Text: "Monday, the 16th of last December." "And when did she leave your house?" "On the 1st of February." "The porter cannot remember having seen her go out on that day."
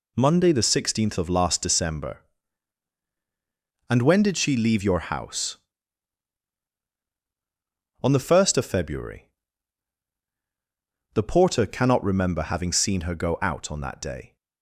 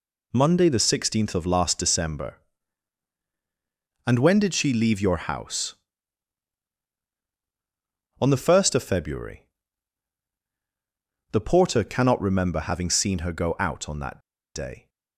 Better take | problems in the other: first | pauses between "that" and "day"; at 14.1 s; 0.36 s long

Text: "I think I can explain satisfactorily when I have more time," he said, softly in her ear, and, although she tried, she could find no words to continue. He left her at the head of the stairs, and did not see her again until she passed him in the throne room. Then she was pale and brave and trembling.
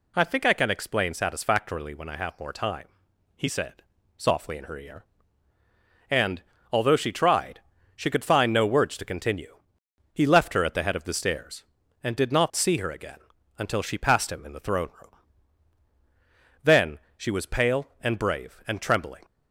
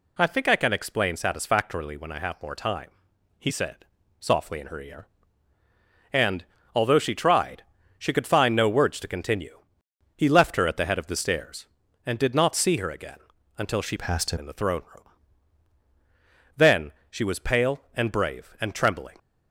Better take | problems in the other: first | pauses between "again" and "until"; at 13.1 s; 0.40 s long; also in the first // changes voice from "passed" to "him"; from 13.9 to 14.3 s; 0.4 s long // pauses between "Then" and "she"; slight; at 16.9 s; 0.18 s long; slight in the first

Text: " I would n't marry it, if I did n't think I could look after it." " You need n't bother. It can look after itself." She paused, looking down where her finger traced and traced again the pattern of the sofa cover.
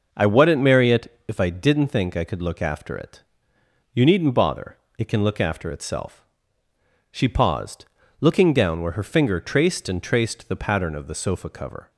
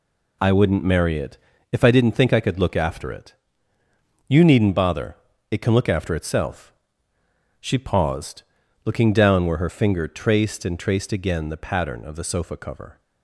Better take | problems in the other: second | skips "again"; at 10.4 s

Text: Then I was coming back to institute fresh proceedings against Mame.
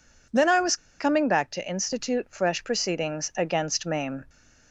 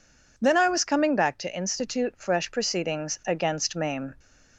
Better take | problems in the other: second | pauses between "was" and "coming"; slight; at 0.7 s; 0.22 s long

